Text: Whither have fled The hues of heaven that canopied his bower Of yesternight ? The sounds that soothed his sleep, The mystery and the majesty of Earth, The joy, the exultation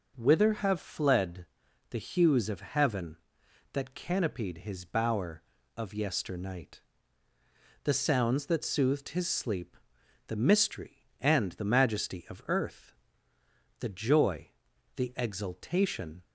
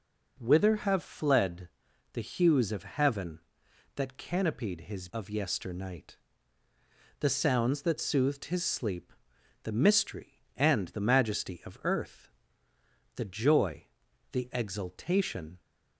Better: first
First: pauses between "fled" and "The"; at 1.4 s; 0.44 s long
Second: pauses between "fled" and "The"; at 1.6 s; 0.44 s long // skips "bower"; at 5.0 s

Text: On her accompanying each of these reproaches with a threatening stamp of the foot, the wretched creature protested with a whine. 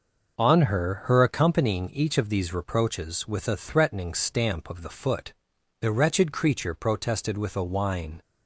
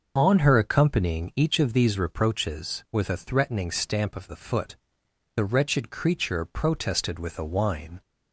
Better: second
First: starts louder than the rest; until 1.4 s; 6 dB // says "her" twice; at 1.0 s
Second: starts louder than the rest; until 1.1 s; 6 dB

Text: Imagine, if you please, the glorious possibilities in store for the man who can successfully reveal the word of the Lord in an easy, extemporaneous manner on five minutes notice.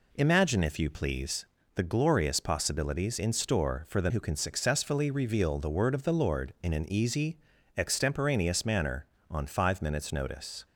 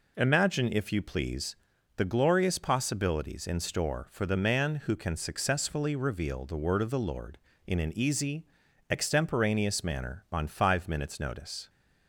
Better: second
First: skips "man"; at 4.0 s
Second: none

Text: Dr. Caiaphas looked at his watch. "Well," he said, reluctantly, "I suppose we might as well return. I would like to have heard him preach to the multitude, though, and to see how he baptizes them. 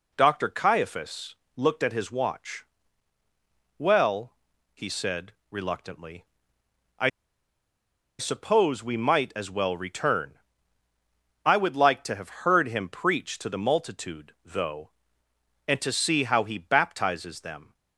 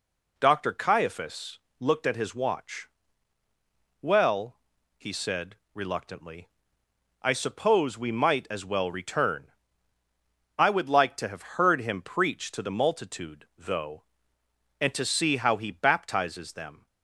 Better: second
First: pauses between "Caiaphas" and "looked"; slight; at 1.3 s; 0.20 s long // pauses between "I" and "suppose"; at 7.0 s; 1.1 s long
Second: pauses between "Caiaphas" and "looked"; slight; at 1.5 s; 0.20 s long

